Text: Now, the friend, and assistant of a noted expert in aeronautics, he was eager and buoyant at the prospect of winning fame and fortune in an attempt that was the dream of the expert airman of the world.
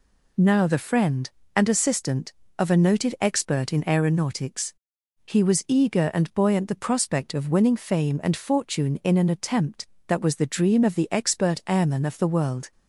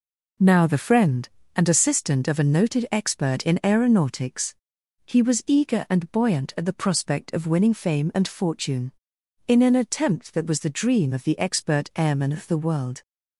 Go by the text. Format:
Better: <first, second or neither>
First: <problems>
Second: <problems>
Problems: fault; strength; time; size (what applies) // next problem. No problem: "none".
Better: second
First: skips "at"; at 6.6 s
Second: none